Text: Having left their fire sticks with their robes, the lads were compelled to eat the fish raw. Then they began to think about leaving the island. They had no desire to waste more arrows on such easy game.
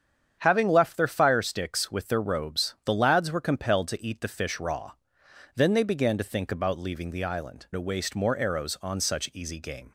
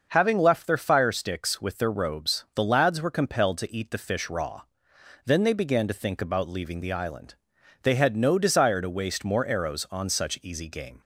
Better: second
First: starts louder than the rest; strong; until 1.4 s; 8 dB // skips "They had no desire"; at 7.6 s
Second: starts louder than the rest; until 1.1 s; 6 dB

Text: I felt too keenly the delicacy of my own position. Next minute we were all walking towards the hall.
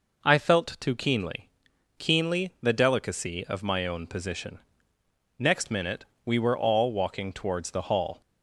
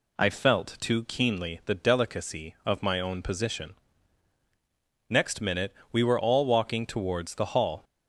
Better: second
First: says "keenly" twice; at 1.9 s // pauses between "minute" and "we"; slight; at 6.0 s; 0.20 s long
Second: pauses between "minute" and "we"; slight; at 5.7 s; 0.18 s long

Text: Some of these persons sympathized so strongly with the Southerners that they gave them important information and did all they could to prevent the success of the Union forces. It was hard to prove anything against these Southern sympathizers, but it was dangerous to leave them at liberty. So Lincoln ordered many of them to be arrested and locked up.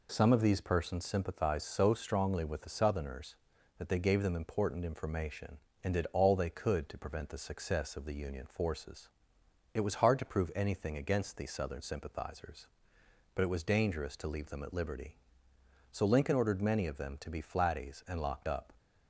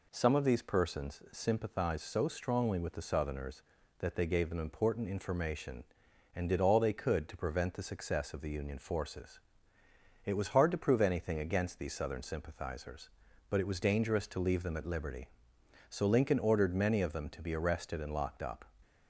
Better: second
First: says "flatties" for "arrested"; at 17.4 s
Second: none

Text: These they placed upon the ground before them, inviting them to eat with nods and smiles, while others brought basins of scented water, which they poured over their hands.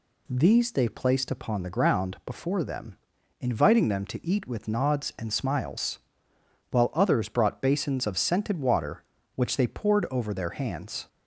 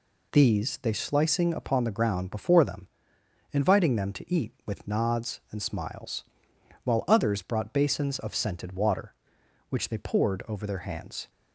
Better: first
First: none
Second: says "slicing" for "placed"; at 0.9 s

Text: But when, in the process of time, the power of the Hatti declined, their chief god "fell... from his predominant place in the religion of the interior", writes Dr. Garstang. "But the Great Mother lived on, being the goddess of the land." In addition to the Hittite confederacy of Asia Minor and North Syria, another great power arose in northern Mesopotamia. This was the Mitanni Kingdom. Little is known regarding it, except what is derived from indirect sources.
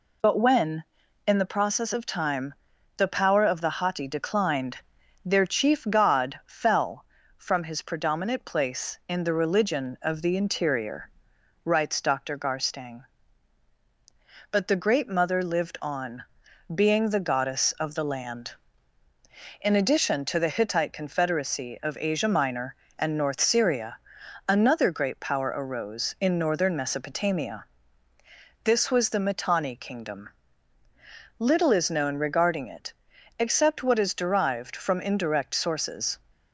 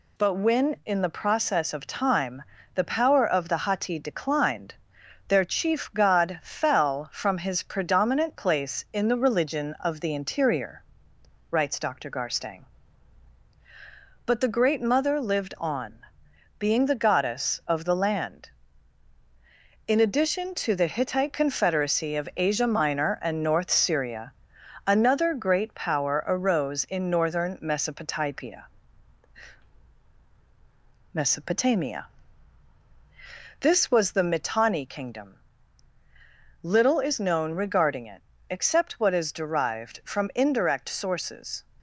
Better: first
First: none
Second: says "Mesopotamia" twice; at 31.1 s

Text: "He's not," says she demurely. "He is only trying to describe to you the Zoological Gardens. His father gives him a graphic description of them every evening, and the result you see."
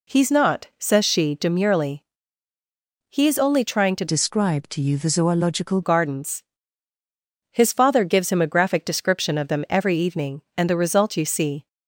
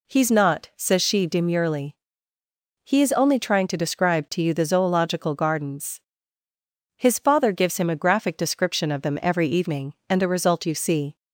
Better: second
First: changes voice from "describe" to "Zoological"; from 4.0 to 5.8 s; 1.8 s long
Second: none

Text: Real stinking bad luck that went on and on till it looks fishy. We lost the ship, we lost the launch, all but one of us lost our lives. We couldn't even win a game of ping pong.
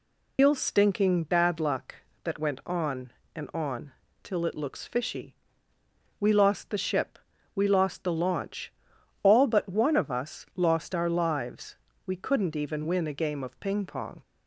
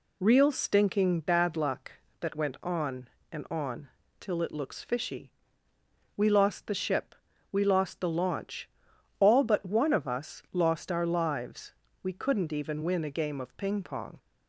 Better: second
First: loses the start of "Real"; at 0.3 s; 150 ms // pauses between "on" and "till"; slight; at 3.9 s; 0.32 s long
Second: pauses between "on" and "till"; slight; at 3.8 s; 0.32 s long

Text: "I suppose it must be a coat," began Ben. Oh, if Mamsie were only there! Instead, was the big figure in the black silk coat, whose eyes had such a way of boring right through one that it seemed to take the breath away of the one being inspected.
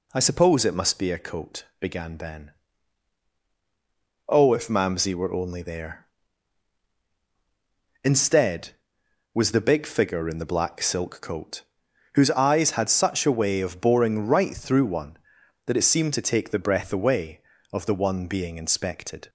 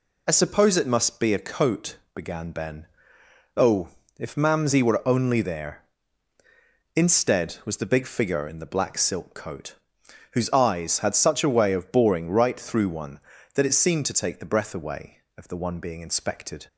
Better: neither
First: none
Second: none

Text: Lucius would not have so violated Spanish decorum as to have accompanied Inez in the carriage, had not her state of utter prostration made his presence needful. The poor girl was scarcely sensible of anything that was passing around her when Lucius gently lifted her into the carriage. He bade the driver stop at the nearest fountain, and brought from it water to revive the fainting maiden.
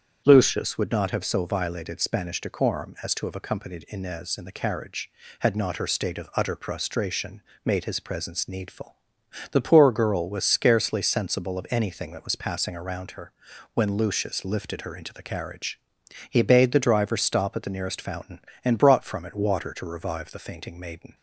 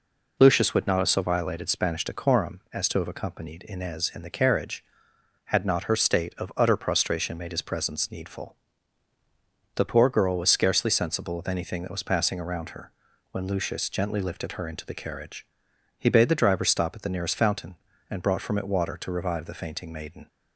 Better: second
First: starts louder than the rest; strong; until 1.2 s; 8 dB // pauses between "prostration" and "made"; slight; at 7.4 s; 0.22 s long // pauses between "her" and "when"; at 13.3 s; 0.44 s long // skips "gently"; at 14.4 s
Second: pauses between "her" and "when"; at 12.9 s; 0.40 s long

